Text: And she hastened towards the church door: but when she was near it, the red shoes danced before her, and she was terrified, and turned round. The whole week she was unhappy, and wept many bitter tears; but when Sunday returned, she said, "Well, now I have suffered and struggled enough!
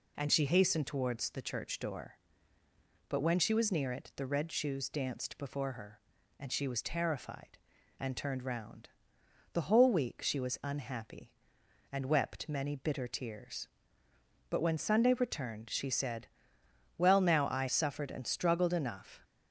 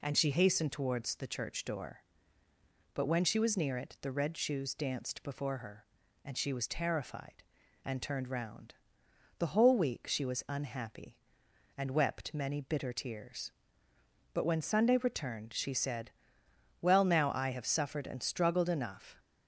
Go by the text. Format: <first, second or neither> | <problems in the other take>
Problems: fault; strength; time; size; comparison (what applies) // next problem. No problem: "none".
second | skips "have"; at 17.6 s